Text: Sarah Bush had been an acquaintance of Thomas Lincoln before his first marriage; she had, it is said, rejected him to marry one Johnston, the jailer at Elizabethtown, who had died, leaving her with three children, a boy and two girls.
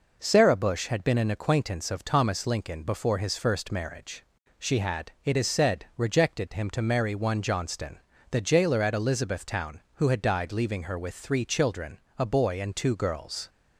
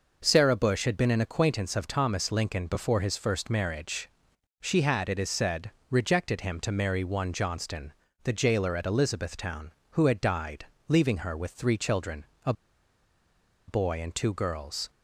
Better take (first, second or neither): first